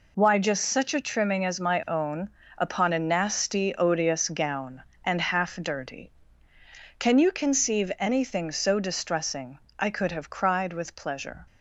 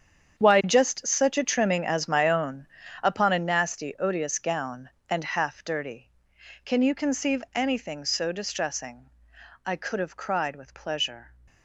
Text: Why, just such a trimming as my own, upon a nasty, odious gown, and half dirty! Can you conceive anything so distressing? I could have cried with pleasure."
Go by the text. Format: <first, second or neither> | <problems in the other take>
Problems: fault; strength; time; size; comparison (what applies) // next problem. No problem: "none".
first | gets quieter; strong; throughout; 13.5 dB